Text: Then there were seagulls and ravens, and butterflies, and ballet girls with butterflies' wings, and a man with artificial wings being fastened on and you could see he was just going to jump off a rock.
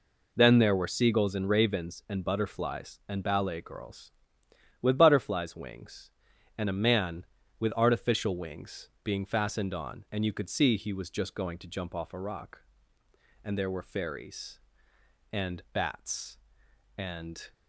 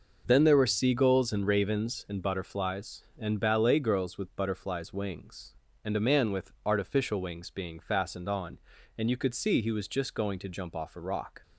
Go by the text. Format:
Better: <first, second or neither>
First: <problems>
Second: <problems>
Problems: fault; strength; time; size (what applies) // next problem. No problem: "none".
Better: second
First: pauses between "wings" and "being"; slight; at 8.8 s; 0.16 s long // goes on to say "And there were fairies and bats and"; strong; from 13.4 s on; 4.0 s long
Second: none